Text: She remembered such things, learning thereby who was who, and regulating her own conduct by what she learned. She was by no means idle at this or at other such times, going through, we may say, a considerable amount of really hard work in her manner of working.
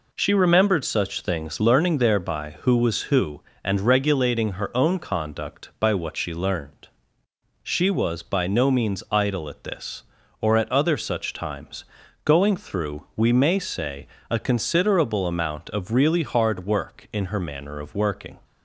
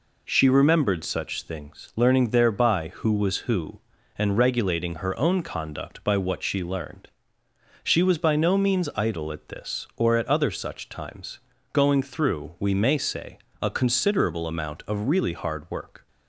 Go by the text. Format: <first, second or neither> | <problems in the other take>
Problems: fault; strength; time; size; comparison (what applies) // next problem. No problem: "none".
first | stops before "in her manner of working"; at 16.0 s